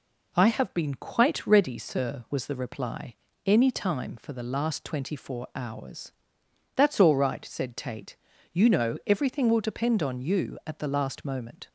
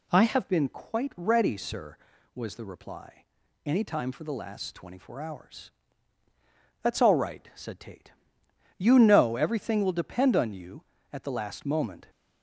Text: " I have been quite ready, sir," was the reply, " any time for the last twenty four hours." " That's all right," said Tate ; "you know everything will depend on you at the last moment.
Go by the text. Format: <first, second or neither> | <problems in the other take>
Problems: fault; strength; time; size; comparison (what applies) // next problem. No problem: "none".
first | changes voice at "been"; from 0.4 s on; 11.6 s long